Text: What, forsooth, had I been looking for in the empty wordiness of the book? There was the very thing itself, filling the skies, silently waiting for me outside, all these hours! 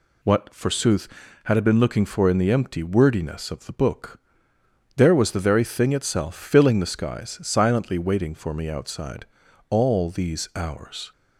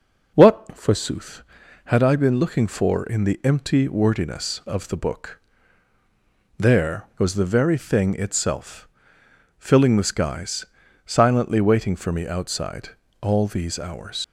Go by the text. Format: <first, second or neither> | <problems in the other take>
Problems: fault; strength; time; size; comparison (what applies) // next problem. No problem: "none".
first | leaves "hours" unfinished; at 14.2 s; 95 ms